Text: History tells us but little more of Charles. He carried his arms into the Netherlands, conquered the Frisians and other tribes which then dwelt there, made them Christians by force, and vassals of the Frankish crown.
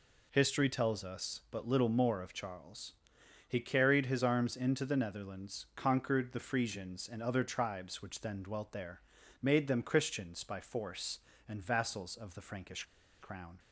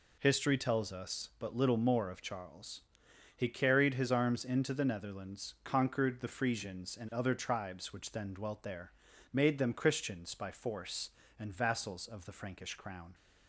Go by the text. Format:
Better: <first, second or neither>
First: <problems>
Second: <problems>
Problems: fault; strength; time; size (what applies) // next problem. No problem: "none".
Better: second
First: pauses between "Frankish" and "crown"; at 12.8 s; 0.37 s long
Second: none